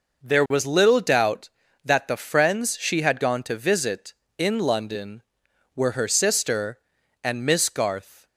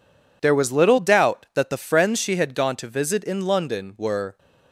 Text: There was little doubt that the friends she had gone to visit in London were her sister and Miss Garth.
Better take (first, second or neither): first